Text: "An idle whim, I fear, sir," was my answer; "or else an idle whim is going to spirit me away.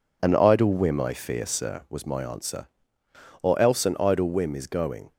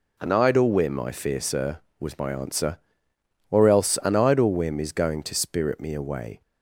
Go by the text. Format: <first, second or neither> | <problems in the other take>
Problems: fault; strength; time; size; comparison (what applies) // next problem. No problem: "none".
second | stops before "to spirit me away"; at 5.1 s